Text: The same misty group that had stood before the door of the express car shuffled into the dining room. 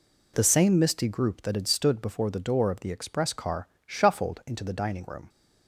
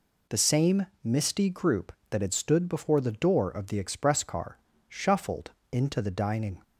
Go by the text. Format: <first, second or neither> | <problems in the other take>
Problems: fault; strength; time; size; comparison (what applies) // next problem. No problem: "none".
first | pauses between "same" and "misty"; slight; at 0.8 s; 0.16 s long // pauses between "car" and "shuffled"; slight; at 4.5 s; 0.30 s long; slight in the first // pauses between "shuffled" and "into"; slight; at 5.5 s; 0.20 s long // stops before "room"; at 6.6 s